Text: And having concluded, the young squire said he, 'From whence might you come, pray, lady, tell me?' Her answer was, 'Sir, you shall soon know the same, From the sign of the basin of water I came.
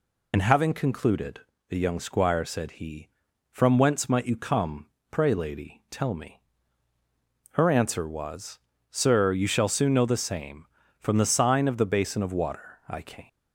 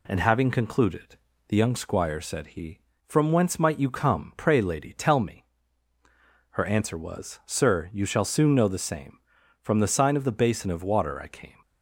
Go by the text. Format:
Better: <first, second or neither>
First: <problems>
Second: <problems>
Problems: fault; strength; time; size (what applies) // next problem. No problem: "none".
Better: second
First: loses the start of "And"; at 0.3 s; 60 ms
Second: none